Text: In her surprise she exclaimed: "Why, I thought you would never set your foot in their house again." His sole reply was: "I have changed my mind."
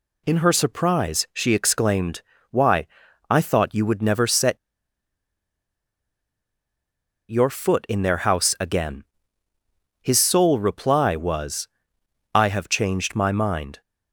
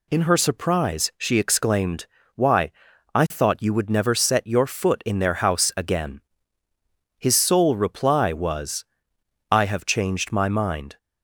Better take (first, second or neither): second